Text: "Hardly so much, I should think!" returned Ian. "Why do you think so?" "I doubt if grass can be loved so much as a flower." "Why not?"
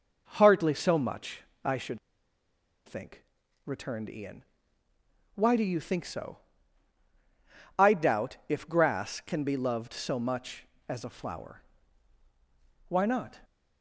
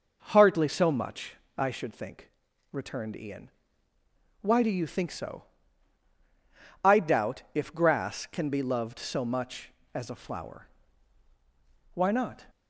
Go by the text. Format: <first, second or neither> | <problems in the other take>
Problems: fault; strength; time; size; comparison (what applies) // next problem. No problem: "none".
second | pauses between "should" and "think"; noticeable; at 1.9 s; 0.87 s long